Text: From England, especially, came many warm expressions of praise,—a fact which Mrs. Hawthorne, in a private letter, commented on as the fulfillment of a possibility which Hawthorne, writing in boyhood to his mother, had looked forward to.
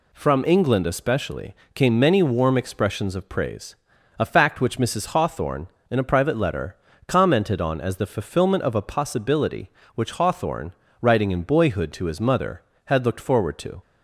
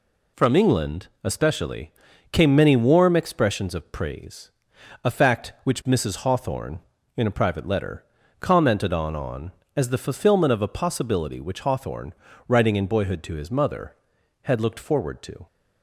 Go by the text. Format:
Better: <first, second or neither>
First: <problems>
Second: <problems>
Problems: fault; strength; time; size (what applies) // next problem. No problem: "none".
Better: first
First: none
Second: says "on" twice; at 9.1 s